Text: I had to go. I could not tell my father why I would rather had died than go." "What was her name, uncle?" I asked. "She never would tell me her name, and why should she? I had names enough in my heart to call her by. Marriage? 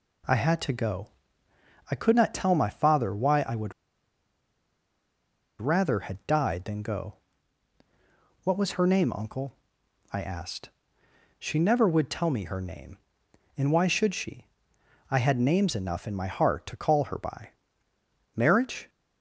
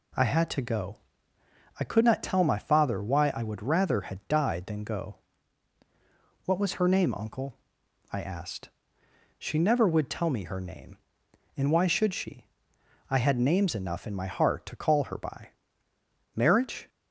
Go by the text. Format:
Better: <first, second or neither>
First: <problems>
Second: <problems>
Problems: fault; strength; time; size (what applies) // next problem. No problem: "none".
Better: second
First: pauses between "would" and "rather"; strong; at 3.7 s; 1.8 s long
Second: none